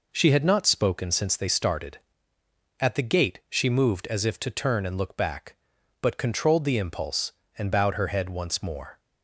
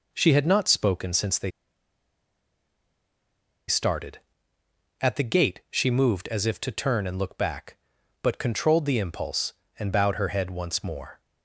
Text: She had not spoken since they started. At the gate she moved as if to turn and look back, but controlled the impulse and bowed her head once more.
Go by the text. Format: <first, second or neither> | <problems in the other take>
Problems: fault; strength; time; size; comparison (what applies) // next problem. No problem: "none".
first | pauses between "they" and "started"; strong; at 1.5 s; 2.1 s long